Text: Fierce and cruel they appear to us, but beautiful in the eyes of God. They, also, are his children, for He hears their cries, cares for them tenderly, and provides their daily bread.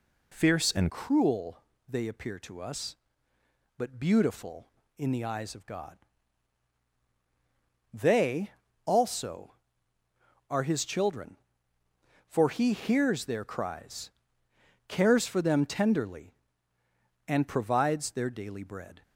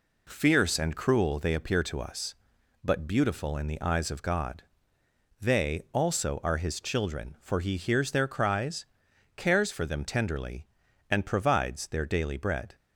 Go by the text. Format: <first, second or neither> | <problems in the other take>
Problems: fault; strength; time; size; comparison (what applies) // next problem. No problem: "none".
second | changes voice at "cruel"; from 0.8 s on; 18.2 s long // pauses between "cruel" and "they"; slight; at 1.5 s; 0.28 s long